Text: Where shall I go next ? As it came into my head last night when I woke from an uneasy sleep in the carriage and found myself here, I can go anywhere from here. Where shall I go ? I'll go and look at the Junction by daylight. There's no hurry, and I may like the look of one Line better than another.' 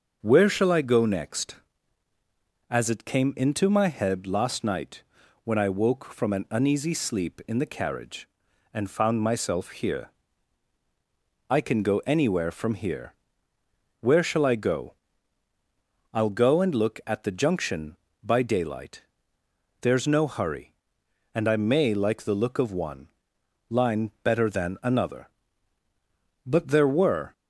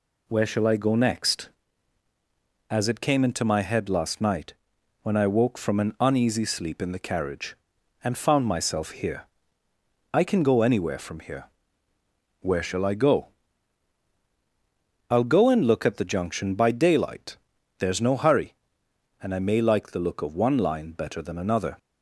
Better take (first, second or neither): second